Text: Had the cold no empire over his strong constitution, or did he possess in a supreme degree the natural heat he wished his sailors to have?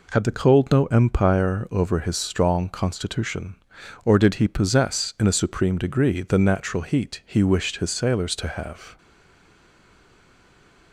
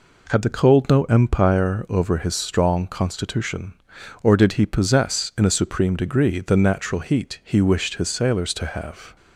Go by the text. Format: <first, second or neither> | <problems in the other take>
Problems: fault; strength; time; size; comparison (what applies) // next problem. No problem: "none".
second | stays silent after the last word; noticeable; from 8.9 s on; 2.0 s long